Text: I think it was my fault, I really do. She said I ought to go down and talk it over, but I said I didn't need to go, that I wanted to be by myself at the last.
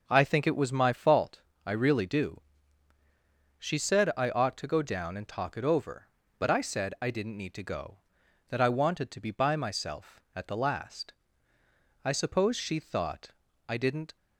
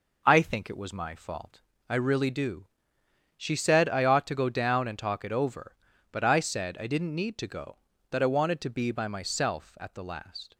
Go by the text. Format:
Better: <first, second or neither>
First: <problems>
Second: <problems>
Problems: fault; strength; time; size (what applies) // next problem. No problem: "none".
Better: second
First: goes on to say "I suppose she thought I didn't"; strong; from 12.0 s on; 2.1 s long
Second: none